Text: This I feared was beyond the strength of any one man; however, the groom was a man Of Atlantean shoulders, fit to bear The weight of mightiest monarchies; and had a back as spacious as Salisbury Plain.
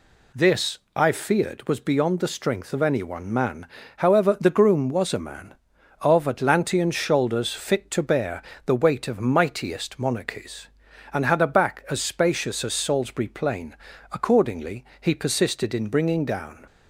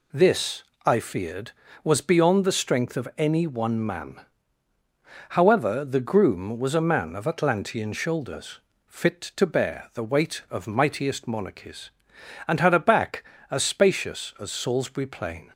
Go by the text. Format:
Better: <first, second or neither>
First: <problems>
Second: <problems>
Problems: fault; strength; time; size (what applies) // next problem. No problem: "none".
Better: second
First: pauses between "This" and "I"; slight; at 0.7 s; 0.16 s long // pauses between "bear" and "The"; slight; at 8.4 s; 0.24 s long // goes on to say "Accordingly he persisted in bringing down"; strong; from 14.1 s on; 2.5 s long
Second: pauses between "This" and "I"; slight; at 0.6 s; 0.24 s long